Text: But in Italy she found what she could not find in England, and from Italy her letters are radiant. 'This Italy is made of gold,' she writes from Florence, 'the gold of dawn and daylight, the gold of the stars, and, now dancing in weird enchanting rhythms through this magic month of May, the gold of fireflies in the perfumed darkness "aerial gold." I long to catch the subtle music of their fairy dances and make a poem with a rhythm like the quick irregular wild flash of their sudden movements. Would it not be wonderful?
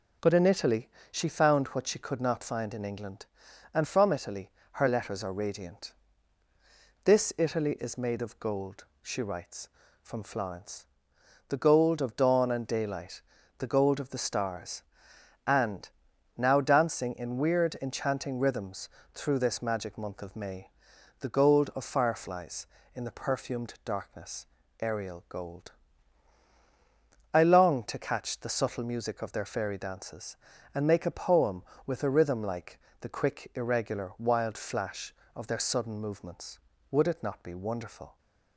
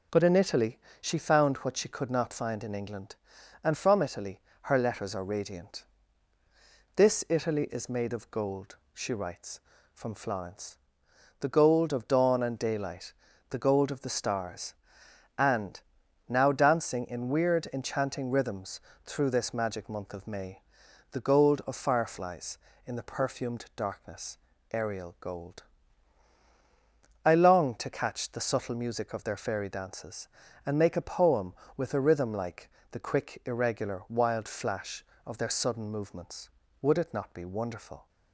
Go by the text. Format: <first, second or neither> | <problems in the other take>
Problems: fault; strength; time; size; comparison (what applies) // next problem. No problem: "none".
neither | pauses between "Italy" and "she"; slight; the same in both // pauses between "Italy" and "her"; slight; the same in both // pauses between "rhythms" and "through"; slight; the same in both // pauses between "darkness" and "aerial"; slight; the same in both // pauses between "like" and "the"; slight; the same in both